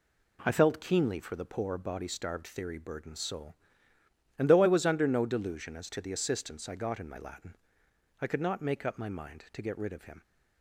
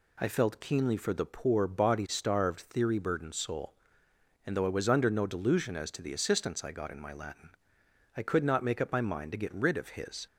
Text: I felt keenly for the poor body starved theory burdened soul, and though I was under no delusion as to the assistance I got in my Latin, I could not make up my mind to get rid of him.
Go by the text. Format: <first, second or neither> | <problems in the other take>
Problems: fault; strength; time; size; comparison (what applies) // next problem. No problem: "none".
first | says "his" for "him"; at 9.9 s